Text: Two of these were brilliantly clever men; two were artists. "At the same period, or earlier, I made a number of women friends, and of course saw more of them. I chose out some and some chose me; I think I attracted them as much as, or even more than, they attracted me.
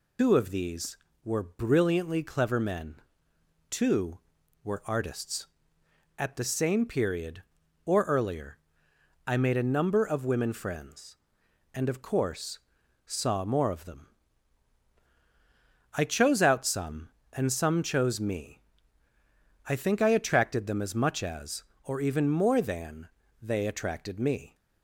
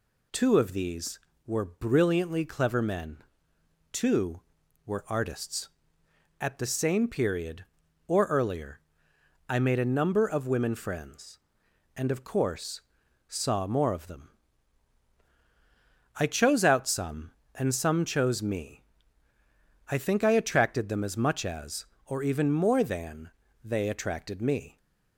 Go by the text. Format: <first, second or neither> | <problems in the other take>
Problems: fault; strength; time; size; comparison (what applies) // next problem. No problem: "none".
second | loses the start of "Two"; at 0.1 s; 100 ms // pauses between "course" and "saw"; noticeable; at 12.5 s; 0.46 s long; noticeable in the second